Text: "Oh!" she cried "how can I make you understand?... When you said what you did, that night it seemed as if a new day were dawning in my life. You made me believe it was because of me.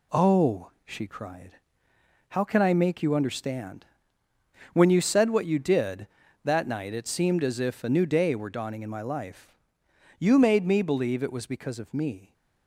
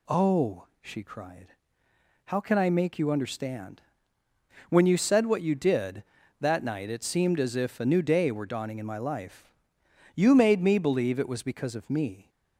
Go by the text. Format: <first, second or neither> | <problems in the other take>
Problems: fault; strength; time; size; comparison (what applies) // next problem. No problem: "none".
second | gets quieter; noticeable; throughout; 4.5 dB // pauses between "cried" and "how"; noticeable; at 1.5 s; 0.78 s long; noticeable in the second